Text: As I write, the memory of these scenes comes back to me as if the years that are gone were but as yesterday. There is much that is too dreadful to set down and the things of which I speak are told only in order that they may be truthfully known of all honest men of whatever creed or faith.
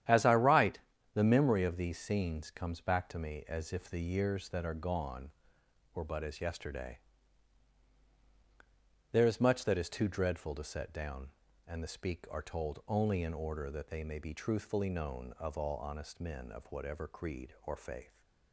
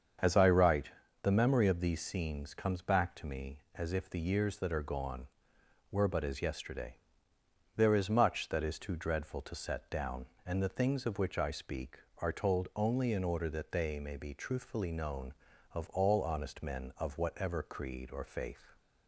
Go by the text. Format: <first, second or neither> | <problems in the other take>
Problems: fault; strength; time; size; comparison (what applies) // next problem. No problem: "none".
second | starts louder than the rest; strong; until 1.4 s; 10.5 dB; strong in the second // skips "things of which I"; at 11.8 s